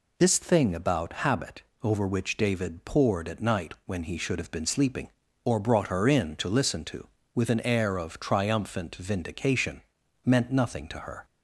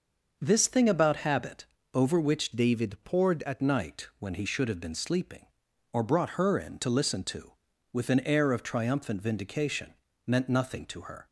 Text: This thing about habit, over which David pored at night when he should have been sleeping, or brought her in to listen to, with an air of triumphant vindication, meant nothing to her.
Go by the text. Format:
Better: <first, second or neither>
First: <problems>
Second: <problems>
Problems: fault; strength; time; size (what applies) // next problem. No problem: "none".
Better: first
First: none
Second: starts louder than the rest; noticeable; until 1.4 s; 6 dB // changes voice from "David" to "at"; from 2.5 to 3.6 s; 1.1 s long